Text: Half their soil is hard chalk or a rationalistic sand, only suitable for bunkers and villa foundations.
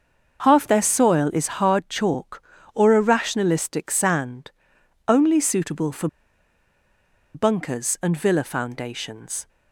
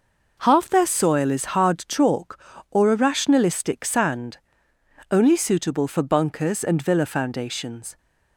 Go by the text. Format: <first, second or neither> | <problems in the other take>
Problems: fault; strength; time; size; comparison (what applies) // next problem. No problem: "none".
second | starts louder than the rest; until 1.4 s; 6.5 dB // pauses between "for" and "bunkers"; strong; at 6.0 s; 1.2 s long